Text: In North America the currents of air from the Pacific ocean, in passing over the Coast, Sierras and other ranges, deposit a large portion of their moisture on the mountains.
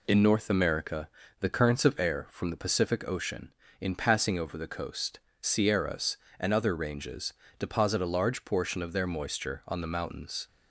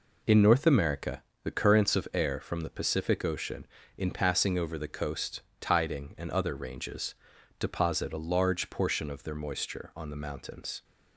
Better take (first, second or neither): first